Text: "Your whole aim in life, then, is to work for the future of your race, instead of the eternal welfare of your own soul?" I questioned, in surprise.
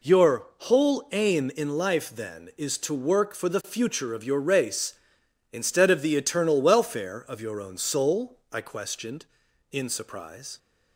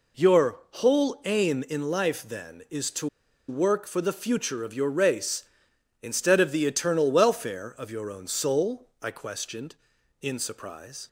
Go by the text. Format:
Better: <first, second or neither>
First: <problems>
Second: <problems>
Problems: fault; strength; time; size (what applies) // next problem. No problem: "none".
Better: first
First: none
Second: pauses between "to" and "work"; at 3.0 s; 0.42 s long